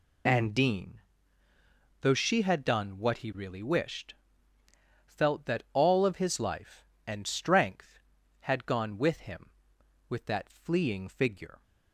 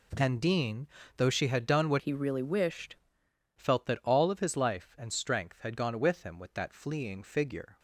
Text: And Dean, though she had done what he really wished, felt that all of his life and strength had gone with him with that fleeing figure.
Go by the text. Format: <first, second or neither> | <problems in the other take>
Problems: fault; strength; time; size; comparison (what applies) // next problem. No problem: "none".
first | changes voice from "he" to "wished"; from 1.9 to 2.9 s; 1.0 s long